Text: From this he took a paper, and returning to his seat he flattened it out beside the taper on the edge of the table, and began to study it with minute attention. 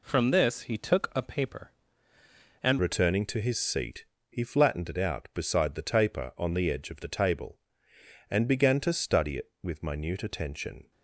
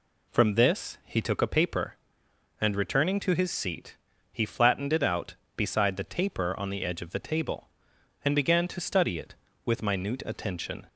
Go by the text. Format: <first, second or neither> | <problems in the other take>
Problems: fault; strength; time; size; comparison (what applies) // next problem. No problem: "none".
second | changes voice at "returning"; from 2.7 s on; 8.2 s long // pauses between "seat" and "he"; slight; at 4.0 s; 0.24 s long; slight in the second